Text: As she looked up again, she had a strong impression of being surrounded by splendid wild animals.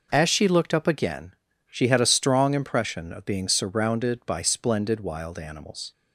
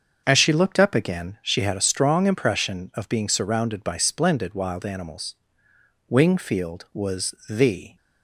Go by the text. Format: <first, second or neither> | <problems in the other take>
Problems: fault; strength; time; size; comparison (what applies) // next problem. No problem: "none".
first | starts louder than the rest; until 1.2 s; 6.5 dB // goes on to say "Wingfield was the"; strong; from 6.0 s on; 1.8 s long